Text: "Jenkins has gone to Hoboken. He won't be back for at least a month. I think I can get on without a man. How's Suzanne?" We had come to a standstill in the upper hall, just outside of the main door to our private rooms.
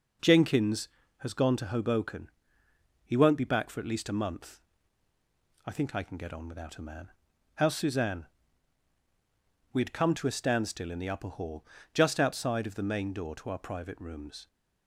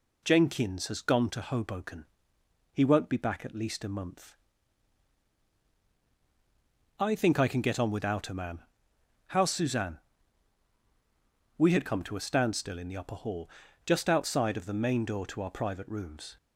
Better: first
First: none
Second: skips "for"; at 3.4 s

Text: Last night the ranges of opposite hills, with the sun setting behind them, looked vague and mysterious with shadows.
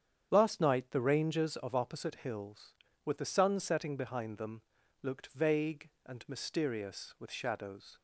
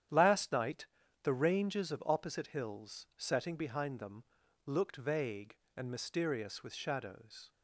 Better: first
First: starts louder than the rest; strong; until 1.3 s; 8.5 dB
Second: starts louder than the rest; strong; until 1.4 s; 10 dB // pauses between "night" and "the"; slight; at 0.8 s; 0.36 s long // skips "with the sun"; at 3.1 s

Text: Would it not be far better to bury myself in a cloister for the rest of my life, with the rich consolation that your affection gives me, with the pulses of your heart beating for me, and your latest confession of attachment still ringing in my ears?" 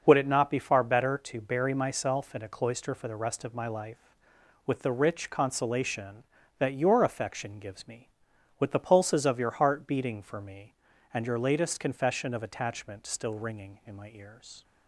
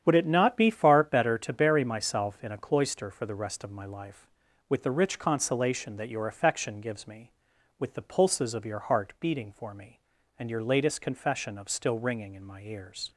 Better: first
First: starts louder than the rest; until 1.0 s; 6.5 dB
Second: starts louder than the rest; strong; until 1.0 s; 8.5 dB // skips "attachment"; at 11.6 s

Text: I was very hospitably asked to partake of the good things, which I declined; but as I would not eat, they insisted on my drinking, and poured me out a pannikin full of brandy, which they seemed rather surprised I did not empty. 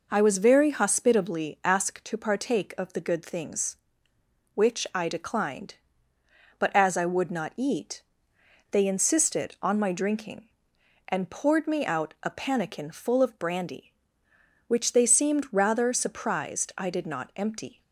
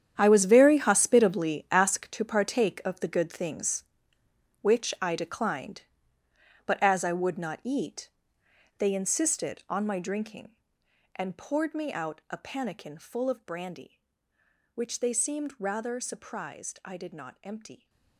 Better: first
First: none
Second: gets quieter; strong; throughout; 14.5 dB

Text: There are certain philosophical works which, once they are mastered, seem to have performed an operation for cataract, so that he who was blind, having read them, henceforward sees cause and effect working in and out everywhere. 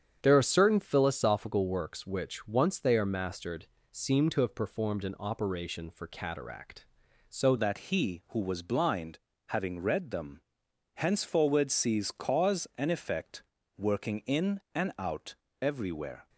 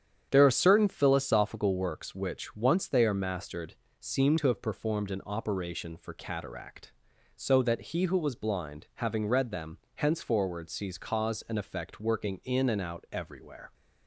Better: second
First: starts louder than the rest; strong; until 1.2 s; 8 dB // changes voice at "that"; from 7.5 s on; 8.7 s long // pauses between "effect" and "working"; slight; at 13.4 s; 0.34 s long // pauses between "out" and "everywhere"; slight; at 15.3 s; 0.26 s long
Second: starts louder than the rest; strong; until 1.3 s; 8.5 dB

